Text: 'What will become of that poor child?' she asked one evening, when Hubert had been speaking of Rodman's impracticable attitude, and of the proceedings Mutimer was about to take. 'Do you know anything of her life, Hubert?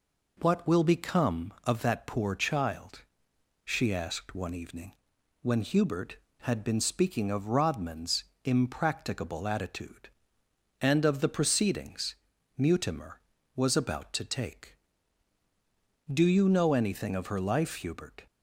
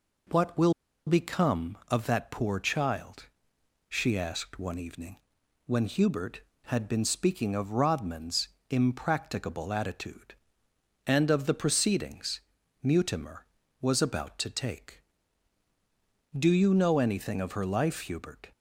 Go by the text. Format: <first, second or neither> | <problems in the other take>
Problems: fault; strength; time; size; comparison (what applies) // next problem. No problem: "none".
first | pauses between "will" and "become"; slight; at 0.7 s; 0.34 s long // pauses between "Rodman's" and "impracticable"; slight; at 8.4 s; 0.22 s long; slight in the first // pauses between "proceedings" and "Mutimer"; at 12.4 s; 0.42 s long; also in the first